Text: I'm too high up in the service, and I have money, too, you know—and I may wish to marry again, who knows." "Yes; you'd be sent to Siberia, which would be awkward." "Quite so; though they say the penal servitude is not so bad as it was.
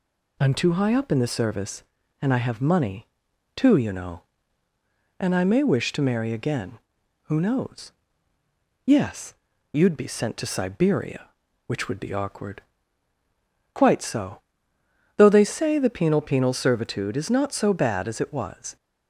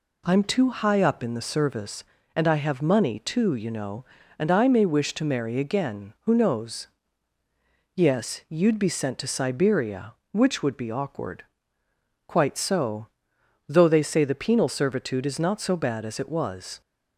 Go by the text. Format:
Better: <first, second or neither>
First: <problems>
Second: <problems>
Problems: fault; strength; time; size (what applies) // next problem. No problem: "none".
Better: second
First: says "penal" twice; at 16.2 s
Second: none